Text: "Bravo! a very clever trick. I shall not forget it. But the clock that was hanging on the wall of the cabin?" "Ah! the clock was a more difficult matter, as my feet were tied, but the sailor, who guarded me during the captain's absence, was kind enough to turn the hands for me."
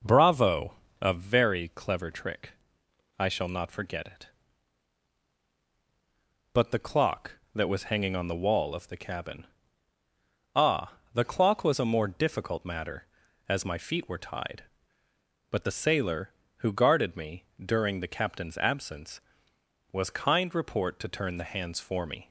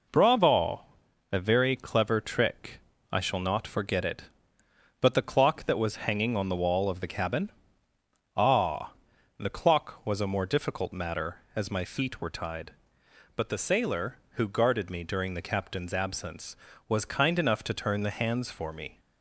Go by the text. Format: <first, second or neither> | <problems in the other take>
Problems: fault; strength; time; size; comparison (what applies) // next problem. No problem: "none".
second | pauses between "me" and "during"; slight; at 17.4 s; 0.20 s long // says "report" for "enough"; at 20.5 s